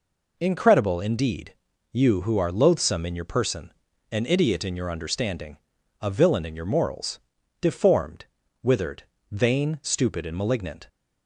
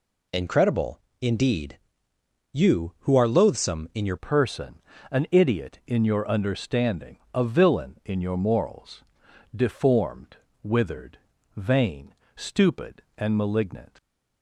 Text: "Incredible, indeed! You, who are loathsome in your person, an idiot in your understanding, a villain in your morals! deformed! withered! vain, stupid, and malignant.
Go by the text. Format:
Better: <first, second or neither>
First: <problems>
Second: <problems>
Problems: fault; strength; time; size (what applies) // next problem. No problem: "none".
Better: first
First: none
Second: changes voice at "person"; from 4.1 s on; 9.9 s long